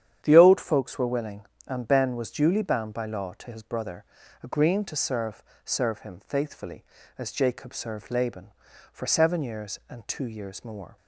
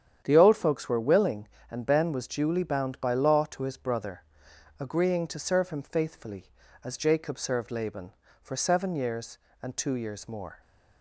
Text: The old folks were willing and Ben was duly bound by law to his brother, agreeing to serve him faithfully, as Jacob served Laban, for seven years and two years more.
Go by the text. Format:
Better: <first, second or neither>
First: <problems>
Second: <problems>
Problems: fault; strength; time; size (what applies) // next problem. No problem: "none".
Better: second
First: starts louder than the rest; strong; until 1.2 s; 9.5 dB // says "serve" twice; at 5.6 s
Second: starts louder than the rest; strong; until 1.2 s; 9 dB